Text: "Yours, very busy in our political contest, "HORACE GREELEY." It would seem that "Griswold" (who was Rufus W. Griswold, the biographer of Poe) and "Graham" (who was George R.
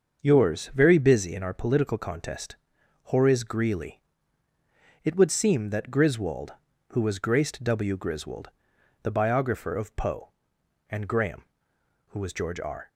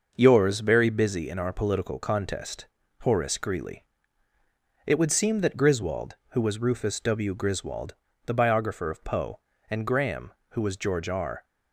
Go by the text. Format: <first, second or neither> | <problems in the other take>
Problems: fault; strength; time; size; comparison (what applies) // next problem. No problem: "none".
second | starts louder than the rest; until 1.2 s; 6.5 dB // says "Graced" for "Rufus"; at 7.1 s